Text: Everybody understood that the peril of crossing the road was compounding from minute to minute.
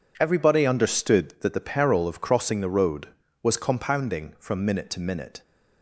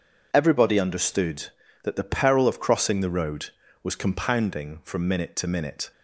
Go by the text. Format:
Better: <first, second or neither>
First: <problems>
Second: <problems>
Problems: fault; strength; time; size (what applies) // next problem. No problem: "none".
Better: neither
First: none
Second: none